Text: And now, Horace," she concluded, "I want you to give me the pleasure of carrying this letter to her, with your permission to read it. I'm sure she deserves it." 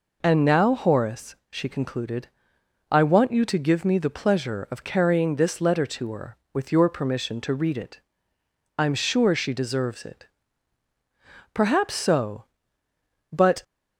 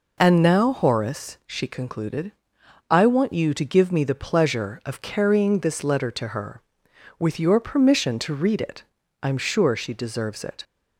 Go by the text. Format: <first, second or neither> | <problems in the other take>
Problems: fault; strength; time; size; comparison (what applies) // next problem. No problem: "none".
second | goes on to say "Perhaps so but"; strong; from 11.5 s on; 2.1 s long